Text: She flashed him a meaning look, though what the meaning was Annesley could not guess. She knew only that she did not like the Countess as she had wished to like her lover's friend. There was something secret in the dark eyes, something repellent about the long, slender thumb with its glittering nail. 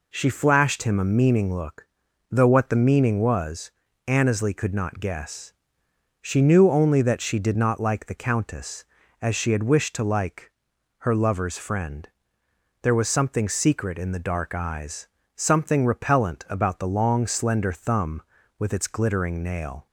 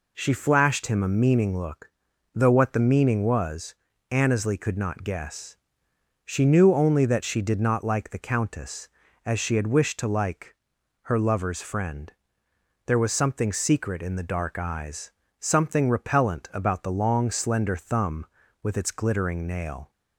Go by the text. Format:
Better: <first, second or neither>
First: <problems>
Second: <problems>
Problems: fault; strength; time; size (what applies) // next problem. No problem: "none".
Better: neither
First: pauses between "was" and "Annesley"; slight; at 3.7 s; 0.36 s long // pauses between "like" and "her"; noticeable; at 10.5 s; 0.48 s long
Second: pauses between "was" and "Annesley"; slight; at 3.7 s; 0.36 s long // pauses between "like" and "her"; noticeable; at 10.5 s; 0.48 s long